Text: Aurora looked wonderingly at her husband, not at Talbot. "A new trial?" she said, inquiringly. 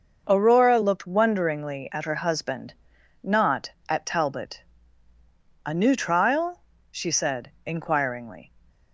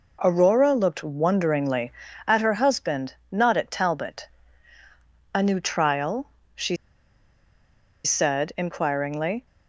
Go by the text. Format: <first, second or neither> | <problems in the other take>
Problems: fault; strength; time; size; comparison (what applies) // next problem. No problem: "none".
first | pauses between "she" and "said"; strong; at 6.7 s; 1.2 s long